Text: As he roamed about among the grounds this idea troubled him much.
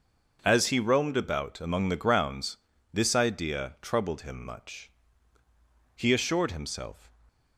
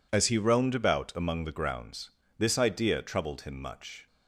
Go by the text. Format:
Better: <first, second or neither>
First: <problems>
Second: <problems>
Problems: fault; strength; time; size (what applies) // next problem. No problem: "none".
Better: second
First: starts louder than the rest; noticeable; until 1.4 s; 6 dB // pauses between "grounds" and "this"; at 2.5 s; 0.38 s long // goes on to say "He assured himself"; noticeable; from 5.9 s on; 1.1 s long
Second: pauses between "grounds" and "this"; slight; at 2.0 s; 0.30 s long